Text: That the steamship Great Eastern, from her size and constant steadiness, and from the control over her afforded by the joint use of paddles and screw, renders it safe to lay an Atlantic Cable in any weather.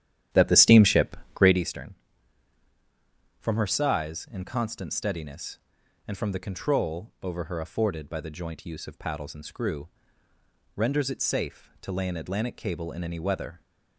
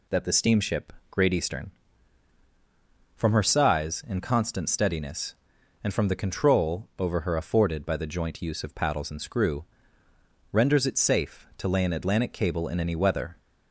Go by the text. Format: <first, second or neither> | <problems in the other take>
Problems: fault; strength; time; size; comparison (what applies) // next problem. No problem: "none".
second | starts louder than the rest; strong; until 1.7 s; 11 dB // pauses between "steamship" and "Great"; slight; at 1.1 s; 0.16 s long; slight in the second